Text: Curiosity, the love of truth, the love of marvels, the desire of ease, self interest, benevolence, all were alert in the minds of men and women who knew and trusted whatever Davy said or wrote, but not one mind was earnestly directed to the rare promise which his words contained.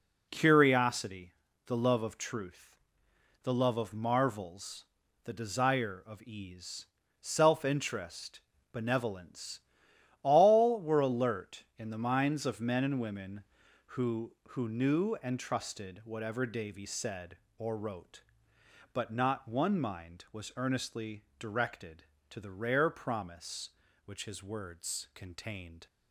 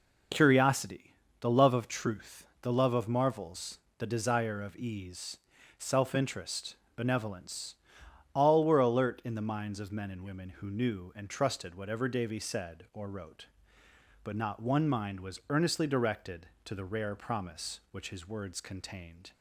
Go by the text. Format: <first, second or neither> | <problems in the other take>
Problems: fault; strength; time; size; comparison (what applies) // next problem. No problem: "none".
second | says "who" twice; at 14.4 s